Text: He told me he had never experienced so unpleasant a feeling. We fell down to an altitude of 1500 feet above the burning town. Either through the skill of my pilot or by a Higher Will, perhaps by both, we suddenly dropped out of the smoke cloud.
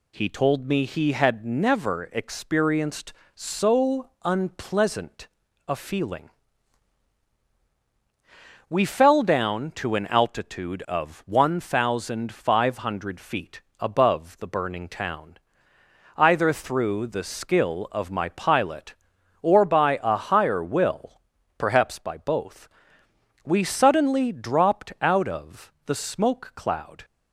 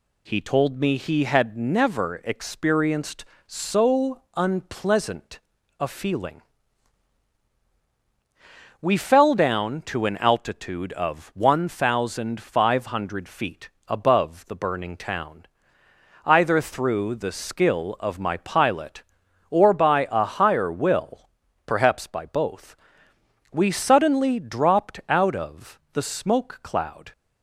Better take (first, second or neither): neither